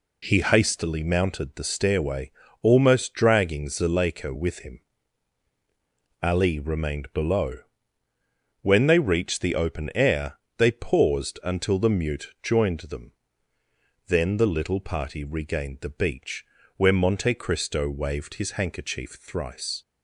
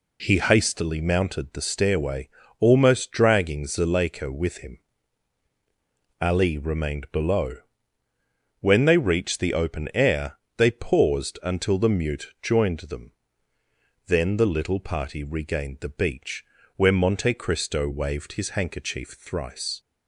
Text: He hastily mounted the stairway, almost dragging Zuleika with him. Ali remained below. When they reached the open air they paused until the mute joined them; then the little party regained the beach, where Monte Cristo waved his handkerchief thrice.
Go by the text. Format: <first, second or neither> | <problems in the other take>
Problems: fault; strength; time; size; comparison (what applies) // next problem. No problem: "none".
neither | pauses between "air" and "they"; slight; the same in both